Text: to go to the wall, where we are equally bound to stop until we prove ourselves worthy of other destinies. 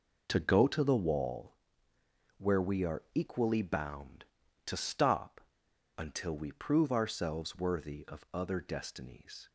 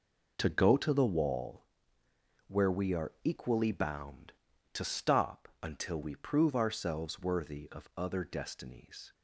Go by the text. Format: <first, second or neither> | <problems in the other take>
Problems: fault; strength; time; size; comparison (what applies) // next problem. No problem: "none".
second | pauses between "stop" and "until"; noticeable; at 5.3 s; 0.57 s long